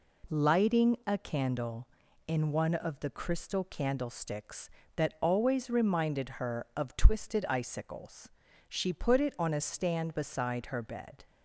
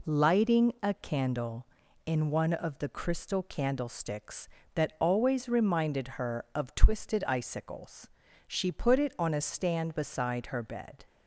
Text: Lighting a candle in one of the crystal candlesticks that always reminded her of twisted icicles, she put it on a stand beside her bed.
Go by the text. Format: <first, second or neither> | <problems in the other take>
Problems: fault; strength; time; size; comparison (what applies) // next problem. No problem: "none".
neither | none